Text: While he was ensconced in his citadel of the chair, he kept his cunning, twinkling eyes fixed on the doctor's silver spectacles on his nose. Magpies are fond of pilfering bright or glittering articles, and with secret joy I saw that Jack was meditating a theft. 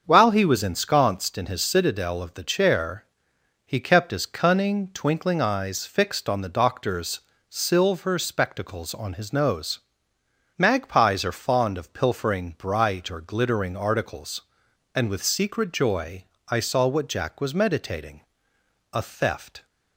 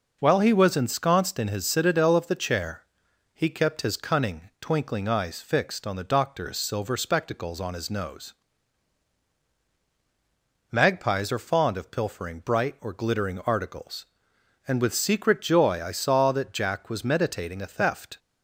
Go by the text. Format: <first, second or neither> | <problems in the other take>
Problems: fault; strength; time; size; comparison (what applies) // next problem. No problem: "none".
second | starts louder than the rest; until 1.0 s; 7 dB // pauses between "doctor's" and "silver"; slight; at 7.2 s; 0.28 s long // pauses between "joy" and "I"; slight; at 16.2 s; 0.24 s long // says "what" for "that"; at 16.8 s // pauses between "meditating" and "a"; noticeable; at 18.2 s; 0.72 s long